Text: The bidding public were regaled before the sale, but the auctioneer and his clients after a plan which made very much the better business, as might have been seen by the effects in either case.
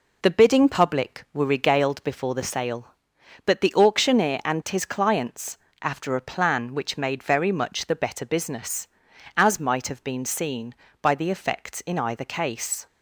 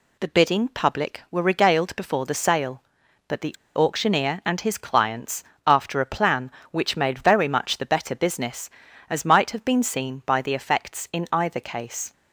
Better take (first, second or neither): first